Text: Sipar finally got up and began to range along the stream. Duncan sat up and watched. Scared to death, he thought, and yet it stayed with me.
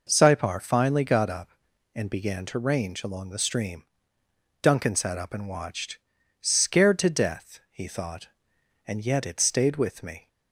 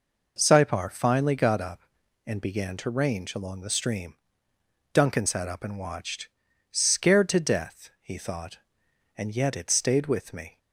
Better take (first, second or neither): neither